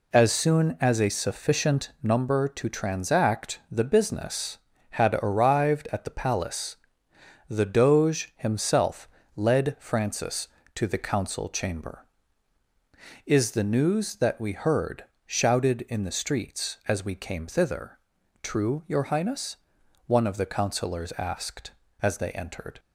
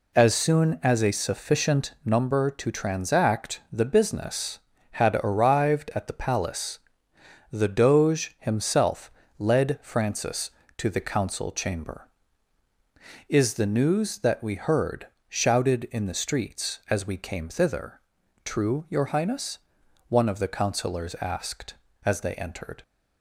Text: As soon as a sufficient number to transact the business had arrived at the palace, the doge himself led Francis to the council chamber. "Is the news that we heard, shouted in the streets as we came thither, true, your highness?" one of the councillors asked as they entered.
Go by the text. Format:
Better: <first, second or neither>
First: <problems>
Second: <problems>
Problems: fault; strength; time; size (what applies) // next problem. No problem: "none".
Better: neither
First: pauses between "himself" and "led"; slight; at 9.0 s; 0.28 s long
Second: pauses between "himself" and "led"; slight; at 9.1 s; 0.28 s long